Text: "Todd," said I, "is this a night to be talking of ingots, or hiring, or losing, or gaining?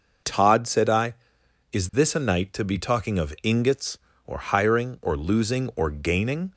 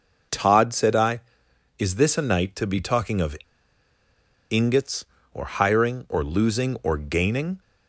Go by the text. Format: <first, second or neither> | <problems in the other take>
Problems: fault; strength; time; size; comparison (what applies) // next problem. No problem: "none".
first | pauses between "of" and "ingots"; at 3.3 s; 1.1 s long